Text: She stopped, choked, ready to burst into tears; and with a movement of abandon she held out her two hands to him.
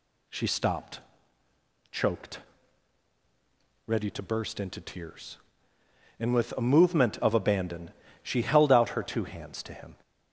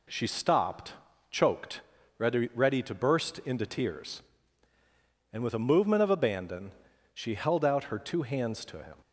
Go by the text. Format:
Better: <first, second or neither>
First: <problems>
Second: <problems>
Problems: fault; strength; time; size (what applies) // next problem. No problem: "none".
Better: first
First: pauses between "abandon" and "she"; slight; at 7.9 s; 0.30 s long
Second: says "ready" twice; at 2.5 s // pauses between "abandon" and "she"; at 6.7 s; 0.42 s long